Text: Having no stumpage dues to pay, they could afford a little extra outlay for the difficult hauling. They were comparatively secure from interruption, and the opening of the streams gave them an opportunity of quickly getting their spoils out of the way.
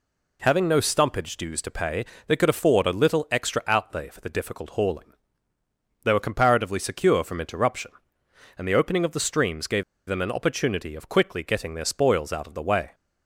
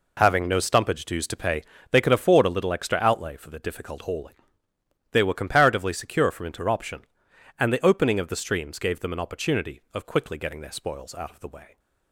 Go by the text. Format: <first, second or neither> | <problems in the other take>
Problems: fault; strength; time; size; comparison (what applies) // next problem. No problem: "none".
second | pauses between "gave" and "them"; slight; at 9.8 s; 0.24 s long